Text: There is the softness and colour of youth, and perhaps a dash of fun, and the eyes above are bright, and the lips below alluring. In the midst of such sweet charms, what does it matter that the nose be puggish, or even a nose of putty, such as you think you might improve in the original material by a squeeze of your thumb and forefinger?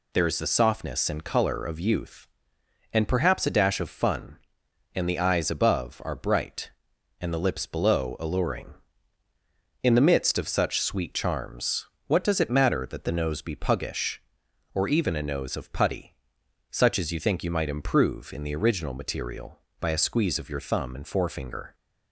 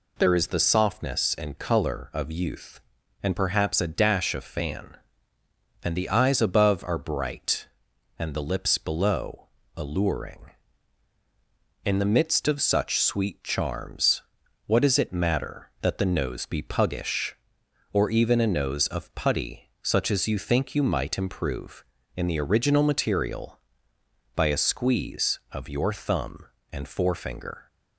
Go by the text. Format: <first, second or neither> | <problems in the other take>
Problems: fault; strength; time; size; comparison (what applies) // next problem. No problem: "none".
first | says "fan" for "fun"; at 4.4 s // pauses between "below" and "alluring"; slight; at 9.4 s; 0.26 s long